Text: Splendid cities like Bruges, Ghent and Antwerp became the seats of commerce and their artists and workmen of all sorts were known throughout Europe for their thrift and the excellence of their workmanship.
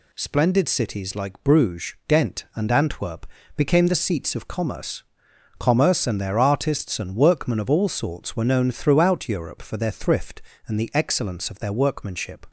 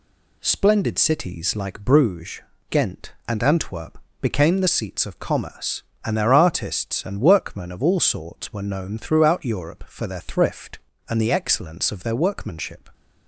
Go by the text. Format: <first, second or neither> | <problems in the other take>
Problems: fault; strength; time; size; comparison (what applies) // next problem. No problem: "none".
second | pauses between "Antwerp" and "became"; slight; at 3.2 s; 0.30 s long; slight in the second // says "commerce" twice; at 5.5 s